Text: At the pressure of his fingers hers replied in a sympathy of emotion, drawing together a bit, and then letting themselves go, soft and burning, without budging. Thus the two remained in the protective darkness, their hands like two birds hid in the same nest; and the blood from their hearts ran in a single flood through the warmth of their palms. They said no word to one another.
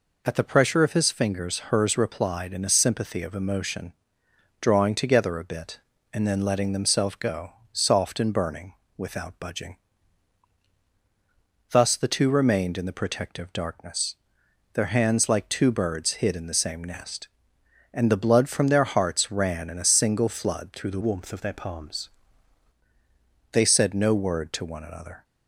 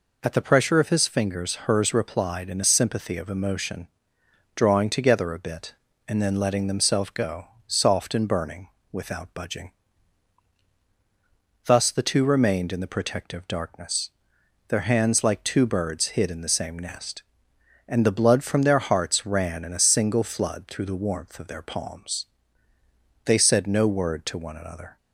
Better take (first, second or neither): second